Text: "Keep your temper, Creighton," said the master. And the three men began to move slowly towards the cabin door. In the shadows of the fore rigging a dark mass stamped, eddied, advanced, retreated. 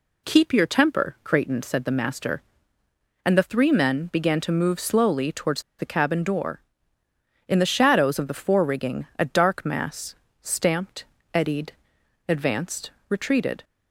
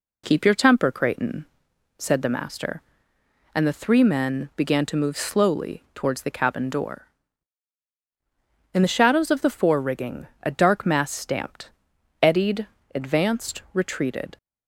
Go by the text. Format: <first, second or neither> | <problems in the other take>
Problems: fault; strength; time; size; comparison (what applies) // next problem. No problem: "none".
second | pauses between "towards" and "the"; slight; at 5.6 s; 0.17 s long // pauses between "mass" and "stamped"; slight; at 10.1 s; 0.26 s long